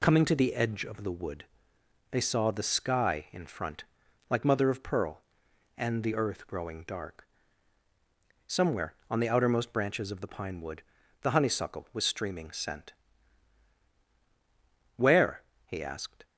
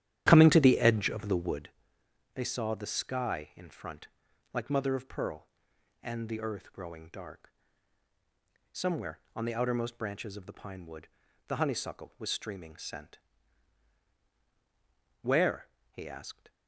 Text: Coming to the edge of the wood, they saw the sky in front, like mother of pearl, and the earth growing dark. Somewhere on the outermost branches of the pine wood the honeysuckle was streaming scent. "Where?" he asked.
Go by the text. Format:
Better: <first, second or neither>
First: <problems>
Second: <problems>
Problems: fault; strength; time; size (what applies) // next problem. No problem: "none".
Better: first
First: pauses between "wood" and "the"; at 10.8 s; 0.40 s long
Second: starts louder than the rest; strong; until 1.8 s; 11.5 dB // pauses between "wood" and "the"; at 11.0 s; 0.40 s long